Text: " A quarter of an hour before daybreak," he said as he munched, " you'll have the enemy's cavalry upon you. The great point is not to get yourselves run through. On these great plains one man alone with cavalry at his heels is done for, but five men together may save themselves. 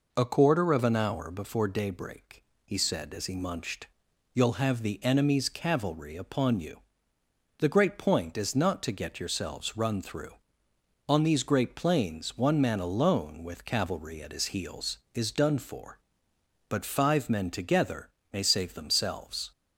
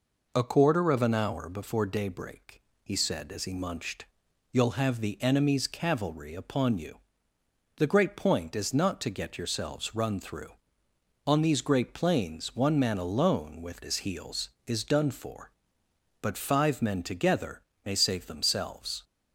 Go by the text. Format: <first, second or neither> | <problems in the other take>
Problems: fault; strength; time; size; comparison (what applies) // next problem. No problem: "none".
first | skips "cavalry at"; at 13.8 s // pauses between "together" and "may"; slight; at 17.6 s; 0.24 s long; slight in the first